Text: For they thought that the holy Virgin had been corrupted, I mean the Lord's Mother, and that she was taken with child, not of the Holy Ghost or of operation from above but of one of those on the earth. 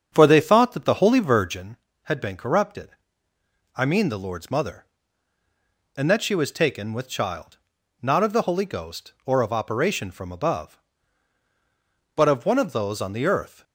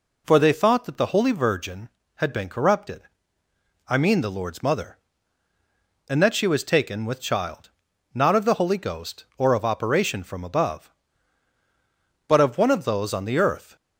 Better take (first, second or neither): second